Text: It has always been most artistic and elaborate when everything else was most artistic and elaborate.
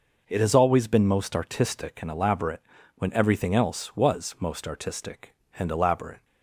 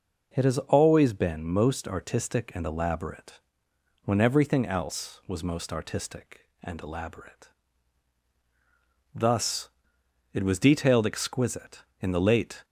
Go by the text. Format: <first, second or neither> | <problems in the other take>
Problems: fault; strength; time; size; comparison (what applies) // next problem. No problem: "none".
first | pauses between "elaborate" and "when"; noticeable; at 3.4 s; 0.64 s long; slight in the first // goes on to say "Thus it was detailed exquisite in the late"; strong; from 9.1 s on; 3.5 s long